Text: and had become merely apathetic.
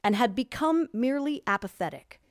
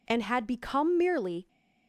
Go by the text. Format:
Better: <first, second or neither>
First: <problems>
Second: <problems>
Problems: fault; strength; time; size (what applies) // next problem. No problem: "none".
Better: first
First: none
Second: stops before "apathetic"; at 1.4 s